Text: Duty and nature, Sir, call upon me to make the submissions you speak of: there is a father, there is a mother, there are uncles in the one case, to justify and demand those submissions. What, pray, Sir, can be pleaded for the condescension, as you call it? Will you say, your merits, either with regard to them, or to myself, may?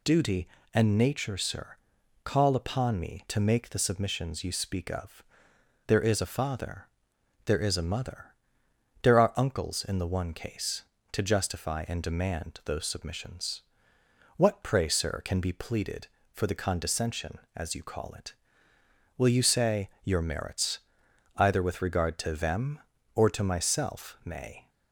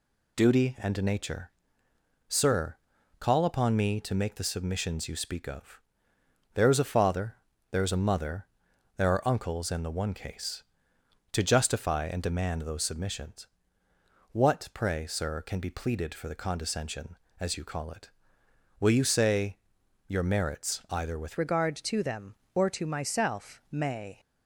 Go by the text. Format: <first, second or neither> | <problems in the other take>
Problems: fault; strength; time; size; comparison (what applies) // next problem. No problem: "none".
first | changes voice at "regard"; from 21.3 s on; 2.8 s long